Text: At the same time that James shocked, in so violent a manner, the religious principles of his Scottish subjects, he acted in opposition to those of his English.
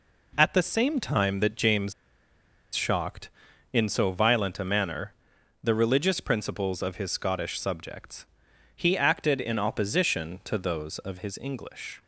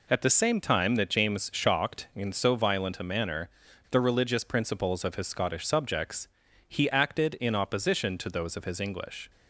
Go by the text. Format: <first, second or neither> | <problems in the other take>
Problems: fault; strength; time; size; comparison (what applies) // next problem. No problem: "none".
second | pauses between "James" and "shocked"; noticeable; at 1.9 s; 0.82 s long